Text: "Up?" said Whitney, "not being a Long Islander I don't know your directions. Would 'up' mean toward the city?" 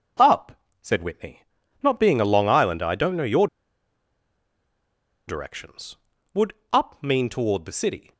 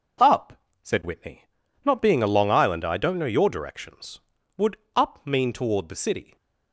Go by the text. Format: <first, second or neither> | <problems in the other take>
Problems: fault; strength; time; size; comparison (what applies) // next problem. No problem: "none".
second | pauses between "your" and "directions"; strong; at 3.4 s; 1.8 s long // pauses between "Would" and "up"; slight; at 6.5 s; 0.18 s long; slight in the second